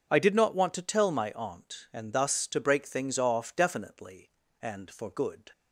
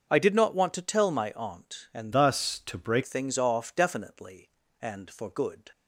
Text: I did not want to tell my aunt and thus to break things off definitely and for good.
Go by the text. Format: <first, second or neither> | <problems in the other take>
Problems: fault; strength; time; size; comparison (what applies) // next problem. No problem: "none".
first | starts louder than the rest; until 1.1 s; 6.5 dB; also in the first // changes voice from "thus" to "break"; from 2.1 to 3.0 s; 0.9 s long